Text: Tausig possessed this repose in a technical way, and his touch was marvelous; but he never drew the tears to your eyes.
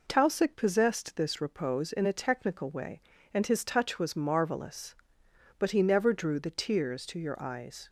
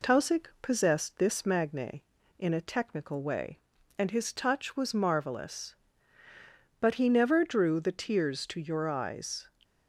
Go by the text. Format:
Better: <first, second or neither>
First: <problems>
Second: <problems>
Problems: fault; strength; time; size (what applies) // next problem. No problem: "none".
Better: first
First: none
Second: says "magne" for "repose"; at 1.4 s